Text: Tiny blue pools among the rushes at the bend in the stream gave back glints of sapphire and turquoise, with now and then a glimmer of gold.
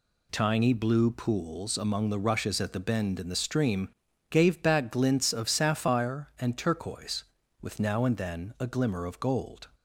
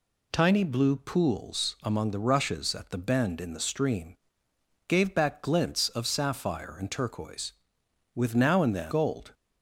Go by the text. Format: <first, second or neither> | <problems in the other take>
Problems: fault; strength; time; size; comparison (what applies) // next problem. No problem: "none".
first | pauses between "stream" and "gave"; noticeable; at 4.1 s; 0.72 s long; also in the first // skips "a glimmer of"; at 8.9 s